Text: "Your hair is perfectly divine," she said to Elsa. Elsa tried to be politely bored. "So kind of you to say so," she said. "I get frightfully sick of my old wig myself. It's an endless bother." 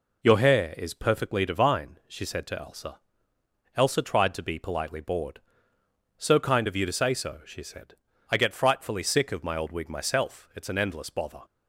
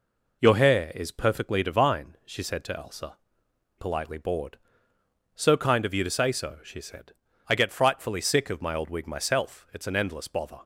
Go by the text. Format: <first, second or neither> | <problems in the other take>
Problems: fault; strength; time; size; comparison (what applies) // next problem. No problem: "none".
first | skips "Elsa tried to be"; at 3.4 s